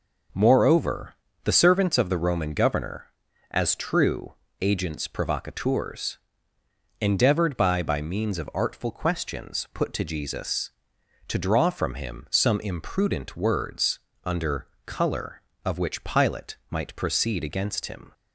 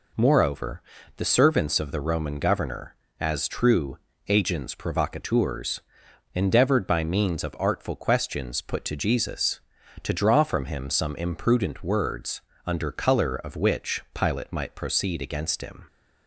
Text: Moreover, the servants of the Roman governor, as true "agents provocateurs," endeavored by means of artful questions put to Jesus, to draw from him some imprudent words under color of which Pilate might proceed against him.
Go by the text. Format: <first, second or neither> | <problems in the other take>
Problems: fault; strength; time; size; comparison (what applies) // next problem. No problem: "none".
second | pauses between "true" and "agents"; slight; at 4.3 s; 0.26 s long; slight in the second // says "by" twice; at 7.8 s // pauses between "words" and "under"; slight; at 13.9 s; 0.24 s long; slight in the second // pauses between "under" and "color"; slight; at 14.6 s; 0.18 s long